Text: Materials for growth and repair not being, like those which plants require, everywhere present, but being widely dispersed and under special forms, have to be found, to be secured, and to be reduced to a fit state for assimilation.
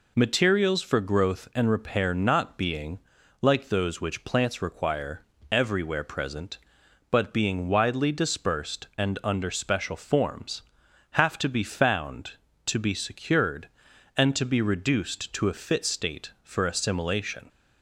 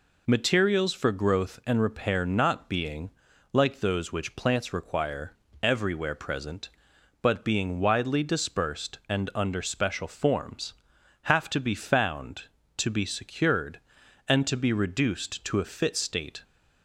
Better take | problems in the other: first | stops before "for assimilation"; at 16.4 s

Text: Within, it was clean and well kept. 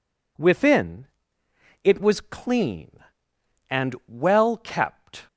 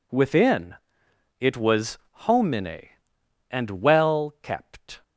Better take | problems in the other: first | says "homine" for "clean"; at 2.1 s

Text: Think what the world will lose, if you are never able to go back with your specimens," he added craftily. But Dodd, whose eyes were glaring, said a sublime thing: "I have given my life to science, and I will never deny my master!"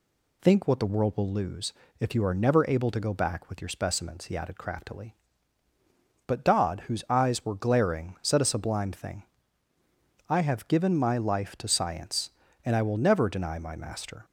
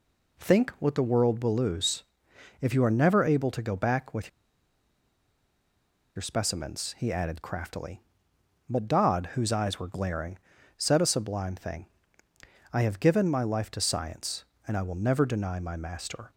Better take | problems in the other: first | pauses between "with" and "your"; strong; at 4.2 s; 1.8 s long

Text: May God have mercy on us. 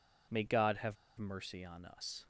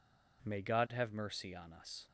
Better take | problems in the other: second | pauses between "have" and "mercy"; slight; at 0.9 s; 0.23 s long

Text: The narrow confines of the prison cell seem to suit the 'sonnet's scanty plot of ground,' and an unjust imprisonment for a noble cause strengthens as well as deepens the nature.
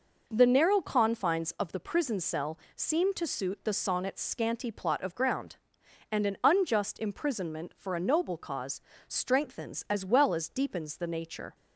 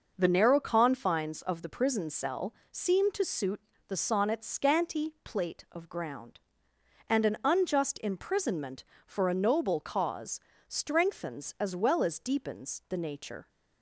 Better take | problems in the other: first | pauses between "cell" and "seem"; slight; at 2.5 s; 0.16 s long; slight in the first // pauses between "suit" and "the"; slight; at 3.5 s; 0.28 s long // says "plate" for "plot"; at 5.2 s // pauses between "cause" and "strengthens"; slight; at 10.3 s; 0.28 s long; slight in the first

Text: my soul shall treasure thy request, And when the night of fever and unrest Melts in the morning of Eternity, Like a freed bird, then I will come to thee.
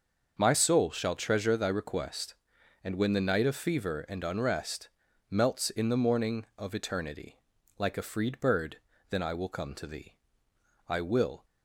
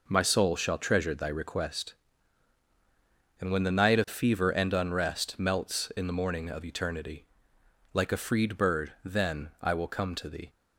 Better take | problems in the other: second | starts louder than the rest; until 1.4 s; 6.5 dB // pauses between "unrest" and "Melts"; at 4.8 s; 0.40 s long // goes on to say "I will"; from 10.8 s on; 0.56 s long

